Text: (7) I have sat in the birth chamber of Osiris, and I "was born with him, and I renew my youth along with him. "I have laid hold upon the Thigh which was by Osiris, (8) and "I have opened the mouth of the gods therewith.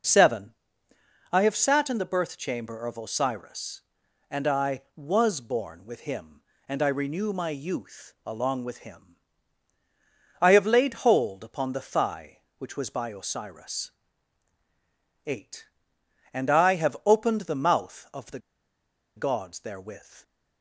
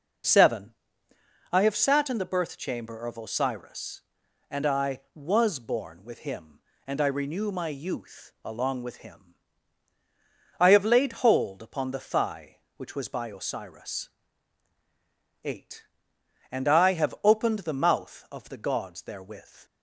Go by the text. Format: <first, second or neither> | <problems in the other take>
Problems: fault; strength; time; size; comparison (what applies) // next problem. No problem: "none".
second | pauses between "the" and "gods"; noticeable; at 18.3 s; 0.77 s long